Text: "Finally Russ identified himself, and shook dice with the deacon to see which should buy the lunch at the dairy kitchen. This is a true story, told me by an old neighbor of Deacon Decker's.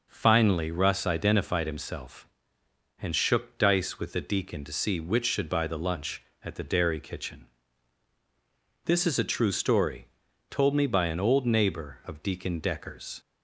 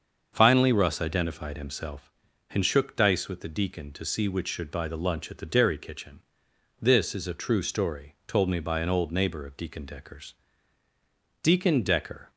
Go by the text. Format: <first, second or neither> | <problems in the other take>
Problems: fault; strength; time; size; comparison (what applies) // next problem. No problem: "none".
first | starts louder than the rest; until 1.3 s; 6.5 dB // goes on to say "Deacon Decker"; noticeable; from 11.4 s on; 0.86 s long